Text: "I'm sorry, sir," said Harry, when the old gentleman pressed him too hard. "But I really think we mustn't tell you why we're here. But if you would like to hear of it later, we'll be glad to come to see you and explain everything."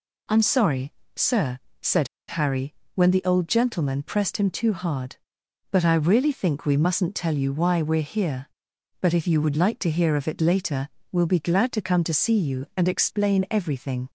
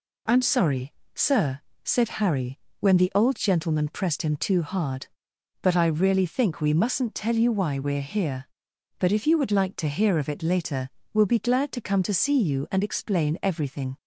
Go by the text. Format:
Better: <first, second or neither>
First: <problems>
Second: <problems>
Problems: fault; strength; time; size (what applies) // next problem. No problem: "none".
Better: second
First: pauses between "said" and "Harry"; slight; at 2.0 s; 0.22 s long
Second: none